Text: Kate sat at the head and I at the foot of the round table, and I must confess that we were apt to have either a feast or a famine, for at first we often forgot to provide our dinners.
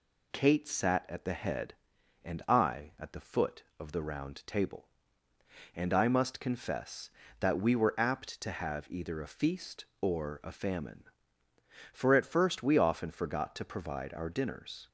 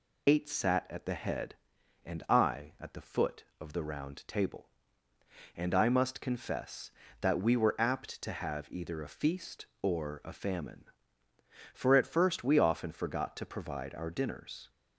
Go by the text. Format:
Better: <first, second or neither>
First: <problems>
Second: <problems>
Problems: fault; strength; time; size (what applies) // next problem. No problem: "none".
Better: first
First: none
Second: loses the start of "Kate"; at 0.2 s; 145 ms